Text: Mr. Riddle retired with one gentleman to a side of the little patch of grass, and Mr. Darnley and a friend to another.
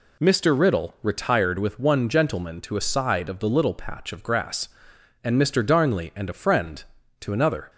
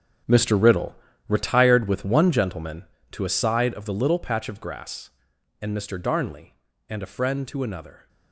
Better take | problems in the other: first | gets quieter; strong; throughout; 13.5 dB // pauses between "Riddle" and "retired"; slight; at 0.9 s; 0.32 s long

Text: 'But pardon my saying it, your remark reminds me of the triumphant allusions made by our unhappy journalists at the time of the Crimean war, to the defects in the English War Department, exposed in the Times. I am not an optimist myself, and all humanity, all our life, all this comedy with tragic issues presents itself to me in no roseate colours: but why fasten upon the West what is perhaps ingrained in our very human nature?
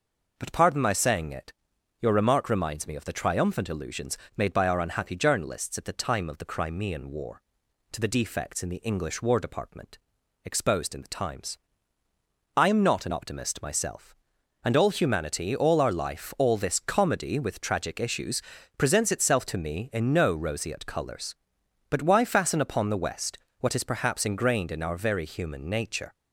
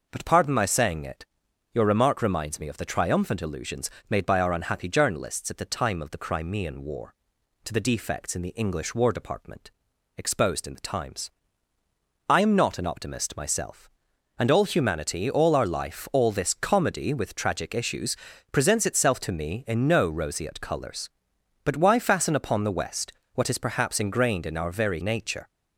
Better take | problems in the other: first | pauses between "allusions" and "made"; slight; at 3.9 s; 0.18 s long; slight in the first // pauses between "issues" and "presents"; slight; at 18.1 s; 0.34 s long; slight in the first // pauses between "West" and "what"; slight; at 23.1 s; 0.24 s long; slight in the first // skips "human"; at 25.0 s

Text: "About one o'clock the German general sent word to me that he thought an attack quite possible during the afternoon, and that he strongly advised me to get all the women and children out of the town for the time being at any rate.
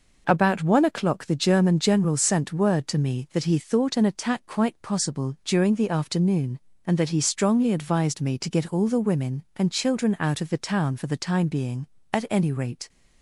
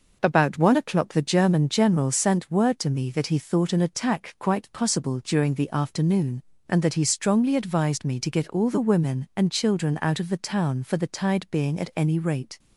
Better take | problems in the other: first | says "tide" for "time"; at 11.0 s

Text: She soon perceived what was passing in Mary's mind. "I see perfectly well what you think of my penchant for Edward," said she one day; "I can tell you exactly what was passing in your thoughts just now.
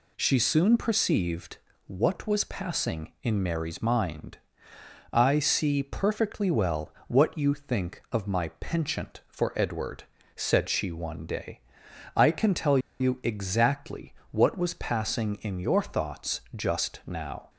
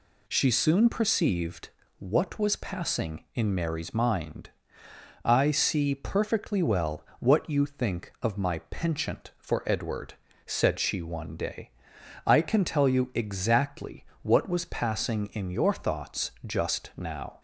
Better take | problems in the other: second | pauses between "perceived" and "what"; slight; at 1.5 s; 0.30 s long; slight in the second // pauses between "well" and "what"; slight; at 6.9 s; 0.16 s long; slight in the second // pauses between "tell" and "you"; slight; at 12.7 s; 0.21 s long // pauses between "exactly" and "what"; slight; at 14.1 s; 0.16 s long; slight in the second

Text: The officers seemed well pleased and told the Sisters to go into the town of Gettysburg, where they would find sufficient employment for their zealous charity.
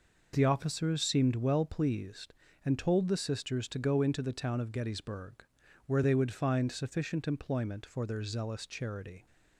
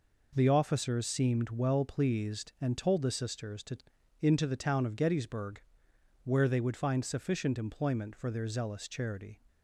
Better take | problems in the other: first | skips "go"; at 3.9 s

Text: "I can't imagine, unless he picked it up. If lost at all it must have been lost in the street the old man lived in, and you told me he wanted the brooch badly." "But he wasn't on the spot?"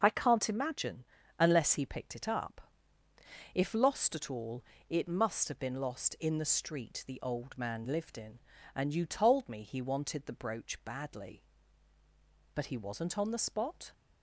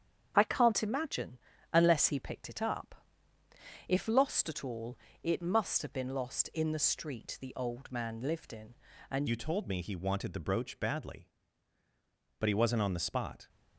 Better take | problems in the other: first | starts louder than the rest; strong; until 1.3 s; 7.5 dB // pauses between "all" and "it"; slight; at 4.9 s; 0.26 s long; slight in the first // changes voice at "you"; from 9.2 s on; 4.2 s long

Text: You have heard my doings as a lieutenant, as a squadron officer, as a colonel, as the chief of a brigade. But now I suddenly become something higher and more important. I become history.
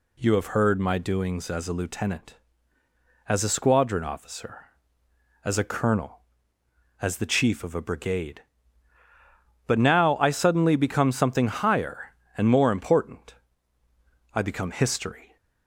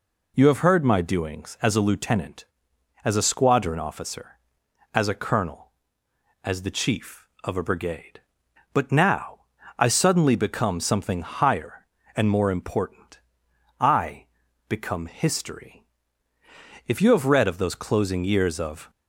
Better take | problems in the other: first | pauses between "now" and "I"; slight; at 9.4 s; 0.36 s long // pauses between "I" and "become"; at 14.2 s; 0.42 s long // goes on to say "If you have read of those closing years of"; strong; from 16.8 s on; 2.0 s long

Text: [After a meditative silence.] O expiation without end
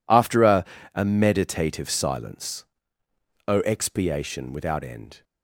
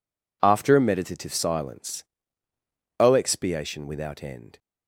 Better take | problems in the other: second | says "a" twice; at 0.9 s

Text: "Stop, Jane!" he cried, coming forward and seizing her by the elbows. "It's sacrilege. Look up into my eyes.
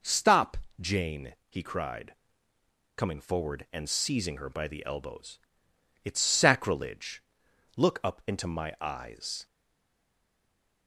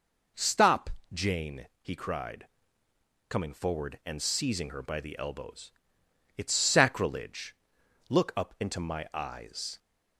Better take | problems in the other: second | stays silent after the last word; noticeable; from 9.4 s on; 1.4 s long

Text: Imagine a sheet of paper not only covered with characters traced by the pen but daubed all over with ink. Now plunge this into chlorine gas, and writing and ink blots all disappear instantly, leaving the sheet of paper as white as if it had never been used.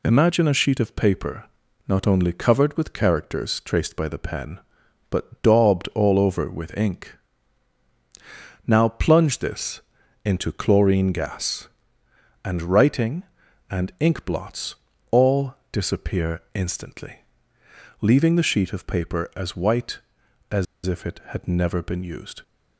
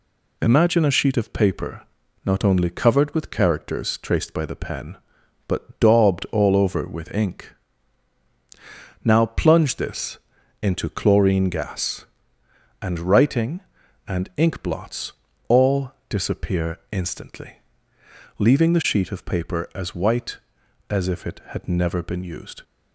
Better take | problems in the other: second | pauses between "paper" and "not"; at 1.4 s; 0.42 s long; also in the second // pauses between "this" and "into"; at 9.8 s; 0.44 s long; also in the second // pauses between "blots" and "all"; at 14.7 s; 0.38 s long; also in the second // pauses between "all" and "disappear"; slight; at 15.5 s; 0.16 s long; slight in the second // pauses between "as" and "if"; slight; at 20.6 s; 0.21 s long

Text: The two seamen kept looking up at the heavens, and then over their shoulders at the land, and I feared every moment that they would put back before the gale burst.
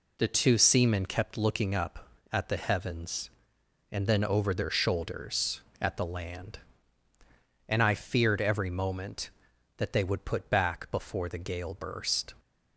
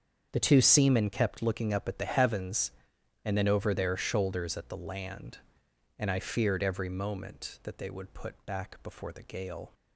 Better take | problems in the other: first | starts louder than the rest; strong; until 1.3 s; 7.5 dB // stops before "burst"; at 9.7 s

